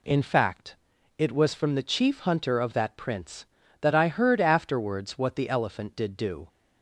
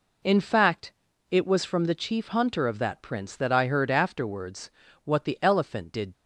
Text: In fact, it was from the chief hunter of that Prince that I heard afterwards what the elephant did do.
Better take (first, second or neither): first